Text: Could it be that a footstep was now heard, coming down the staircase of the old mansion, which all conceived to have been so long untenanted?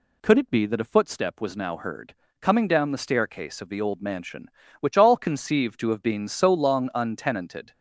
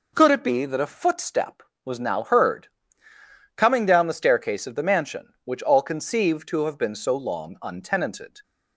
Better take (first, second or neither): first